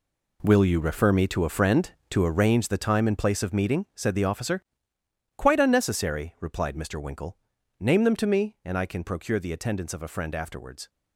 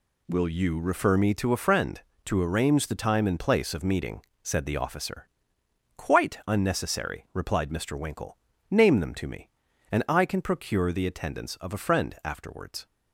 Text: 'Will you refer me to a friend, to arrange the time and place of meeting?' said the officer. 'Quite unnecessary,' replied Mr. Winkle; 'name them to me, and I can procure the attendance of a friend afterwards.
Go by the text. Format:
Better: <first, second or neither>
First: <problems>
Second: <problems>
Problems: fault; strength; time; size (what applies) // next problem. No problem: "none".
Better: second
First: gets quieter; strong; throughout; 12 dB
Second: none